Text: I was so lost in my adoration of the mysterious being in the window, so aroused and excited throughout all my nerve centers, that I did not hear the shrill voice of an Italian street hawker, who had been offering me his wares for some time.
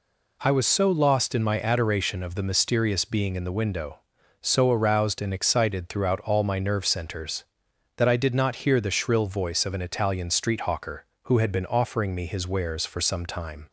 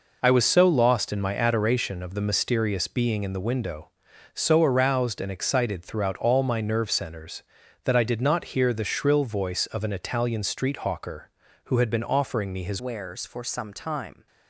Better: first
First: none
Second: changes voice at "wares"; from 12.7 s on; 1.5 s long

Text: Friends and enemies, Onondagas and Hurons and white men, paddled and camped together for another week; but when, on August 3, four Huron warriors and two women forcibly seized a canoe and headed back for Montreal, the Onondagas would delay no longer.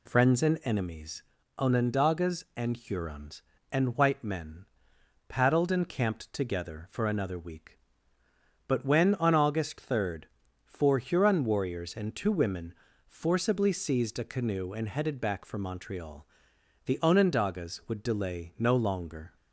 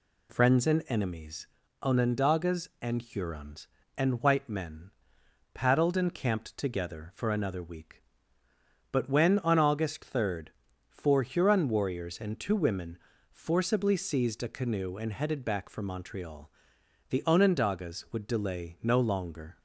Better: neither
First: pauses between "women" and "forcibly"; slight; at 12.7 s; 0.32 s long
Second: pauses between "women" and "forcibly"; slight; at 12.9 s; 0.32 s long

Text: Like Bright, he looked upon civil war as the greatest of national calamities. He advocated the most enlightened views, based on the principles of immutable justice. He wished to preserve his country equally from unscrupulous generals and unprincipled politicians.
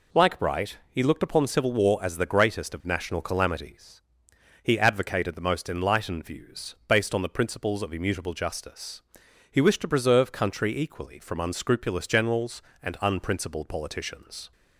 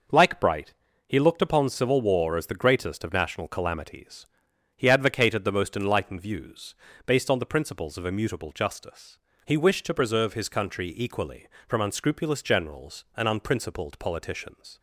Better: second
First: skips "his"; at 10.3 s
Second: none

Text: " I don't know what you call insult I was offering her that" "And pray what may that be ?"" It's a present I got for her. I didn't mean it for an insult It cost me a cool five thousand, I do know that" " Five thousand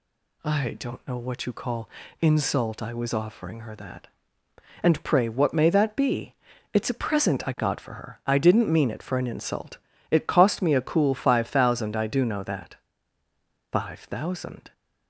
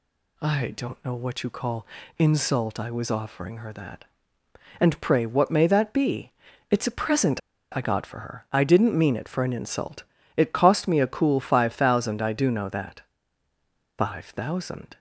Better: first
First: pauses between "call" and "insult"; slight; at 1.8 s; 0.32 s long // pauses between "insult" and "It"; slight; at 9.7 s; 0.34 s long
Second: pauses between "call" and "insult"; slight; at 1.8 s; 0.32 s long // pauses between "present" and "I"; slight; at 7.3 s; 0.34 s long // pauses between "insult" and "It"; slight; at 10.0 s; 0.34 s long

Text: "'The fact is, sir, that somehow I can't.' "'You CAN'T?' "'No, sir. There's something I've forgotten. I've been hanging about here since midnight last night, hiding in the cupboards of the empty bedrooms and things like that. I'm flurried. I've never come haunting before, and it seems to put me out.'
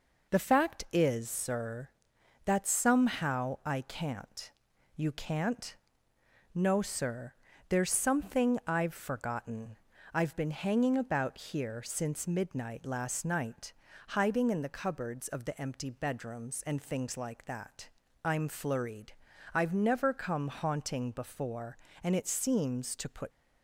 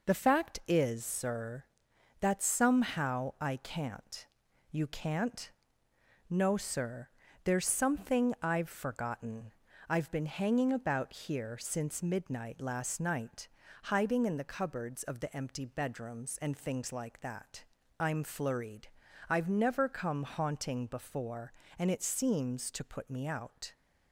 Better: second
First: stops before "me out"; at 23.3 s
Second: none

